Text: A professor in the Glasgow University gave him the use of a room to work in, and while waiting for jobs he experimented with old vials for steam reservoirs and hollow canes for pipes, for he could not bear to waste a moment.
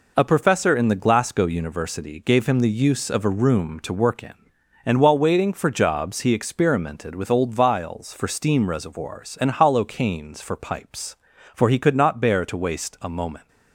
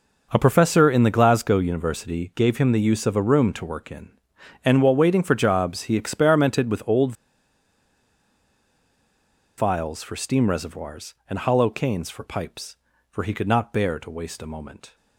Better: first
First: none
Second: pauses between "old" and "vials"; strong; at 7.1 s; 2.4 s long

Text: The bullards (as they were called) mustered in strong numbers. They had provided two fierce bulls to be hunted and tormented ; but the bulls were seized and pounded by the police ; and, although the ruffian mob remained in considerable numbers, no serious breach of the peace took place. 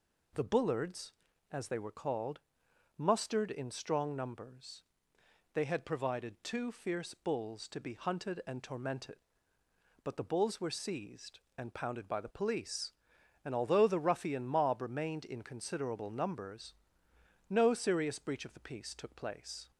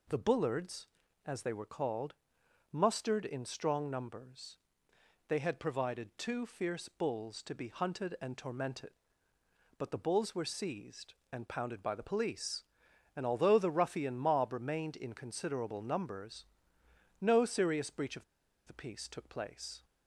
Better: first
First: none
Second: pauses between "of" and "the"; at 18.2 s; 0.42 s long

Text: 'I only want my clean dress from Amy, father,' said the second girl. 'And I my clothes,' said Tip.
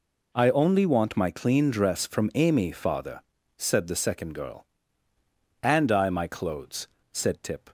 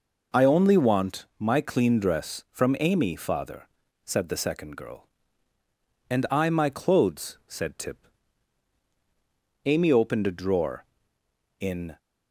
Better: first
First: none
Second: goes on to say "Amy opened a drawer in"; strong; from 9.6 s on; 2.3 s long

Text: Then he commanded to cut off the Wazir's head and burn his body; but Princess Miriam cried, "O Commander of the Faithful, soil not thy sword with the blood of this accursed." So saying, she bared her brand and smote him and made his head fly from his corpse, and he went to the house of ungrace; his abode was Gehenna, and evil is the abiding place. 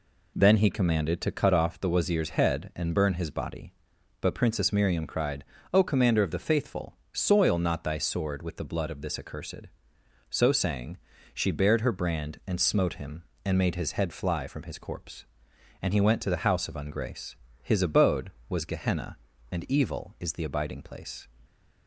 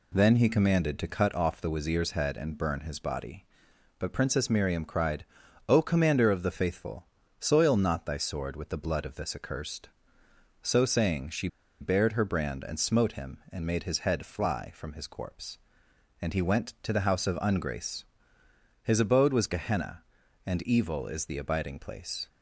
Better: first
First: none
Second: pauses between "she" and "bared"; slight; at 11.4 s; 0.33 s long

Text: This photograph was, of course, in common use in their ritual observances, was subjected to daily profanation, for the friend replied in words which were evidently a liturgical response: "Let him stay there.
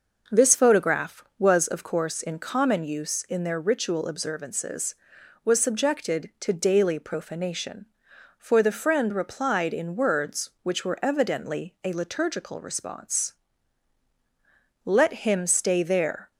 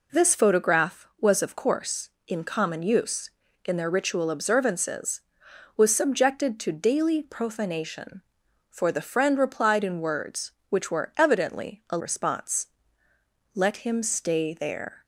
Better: first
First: none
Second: skips "liturgical"; at 11.9 s

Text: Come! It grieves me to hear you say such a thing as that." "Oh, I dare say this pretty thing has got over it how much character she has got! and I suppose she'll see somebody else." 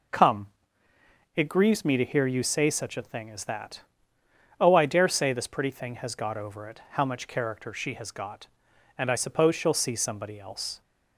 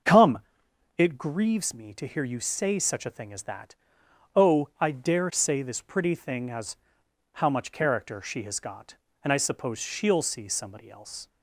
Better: first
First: none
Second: starts louder than the rest; until 1.6 s; 6.5 dB // skips "got over it"; at 7.0 s

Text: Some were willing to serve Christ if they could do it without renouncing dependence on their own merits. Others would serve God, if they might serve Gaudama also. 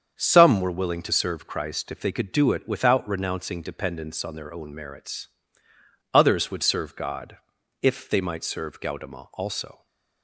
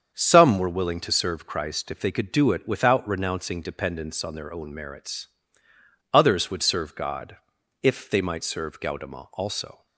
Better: neither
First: starts louder than the rest; strong; until 1.1 s; 7.5 dB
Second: starts louder than the rest; strong; until 1.1 s; 7.5 dB

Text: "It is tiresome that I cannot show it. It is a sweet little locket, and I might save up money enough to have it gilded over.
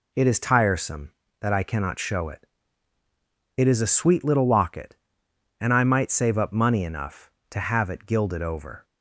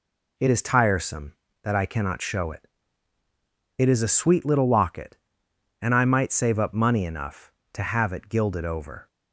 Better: neither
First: none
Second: none

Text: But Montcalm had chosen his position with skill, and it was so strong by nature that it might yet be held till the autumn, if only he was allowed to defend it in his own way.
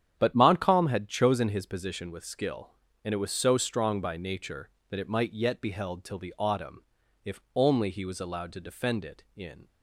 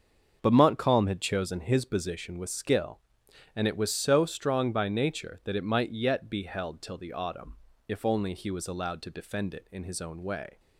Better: second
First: starts louder than the rest; strong; until 1.2 s; 9.5 dB // pauses between "if" and "only"; slight; at 7.3 s; 0.16 s long // stops before "his own way"; at 9.6 s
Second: starts louder than the rest; until 1.4 s; 7 dB

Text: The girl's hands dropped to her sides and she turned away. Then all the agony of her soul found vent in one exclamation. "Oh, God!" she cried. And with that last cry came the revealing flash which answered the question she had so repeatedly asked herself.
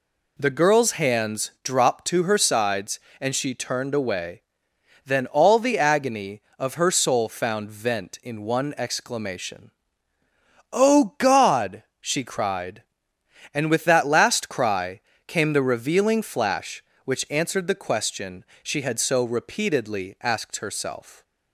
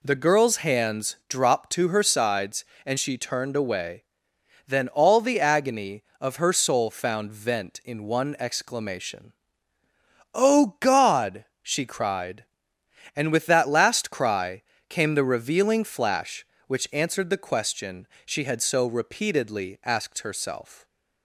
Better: neither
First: pauses between "cry" and "came"; slight; at 14.9 s; 0.26 s long // pauses between "question" and "she"; slight; at 18.4 s; 0.16 s long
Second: pauses between "cry" and "came"; slight; at 14.6 s; 0.26 s long // pauses between "question" and "she"; slight; at 18.0 s; 0.16 s long

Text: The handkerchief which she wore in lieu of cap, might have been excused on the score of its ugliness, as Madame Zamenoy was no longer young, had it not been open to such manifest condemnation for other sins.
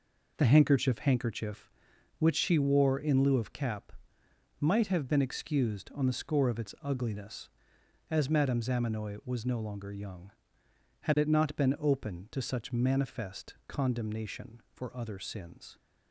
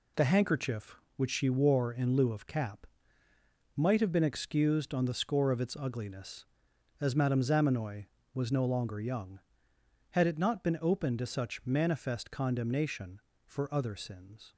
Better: second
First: says "handkerchief" twice; at 0.9 s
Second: none

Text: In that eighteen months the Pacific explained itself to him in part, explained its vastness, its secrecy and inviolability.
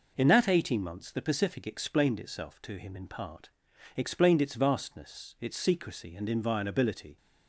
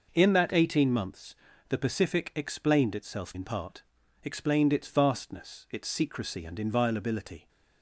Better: first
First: none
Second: pauses between "months" and "the"; slight; at 1.3 s; 0.32 s long // skips "to him"; at 3.3 s

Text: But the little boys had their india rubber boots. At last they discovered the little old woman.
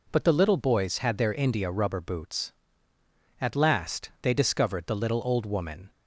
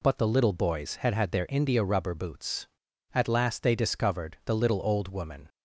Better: first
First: none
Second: says "had" twice; at 1.1 s

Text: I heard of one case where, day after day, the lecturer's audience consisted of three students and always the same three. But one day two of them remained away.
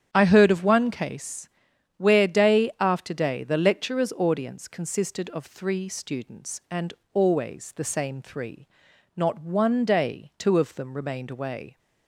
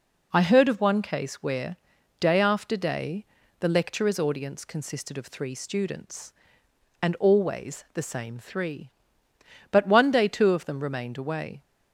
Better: second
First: starts louder than the rest; strong; until 1.1 s; 9.5 dB // pauses between "case" and "where"; noticeable; at 1.4 s; 0.48 s long // pauses between "and" and "always"; slight; at 6.9 s; 0.18 s long // says "Not" for "But"; at 9.1 s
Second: none

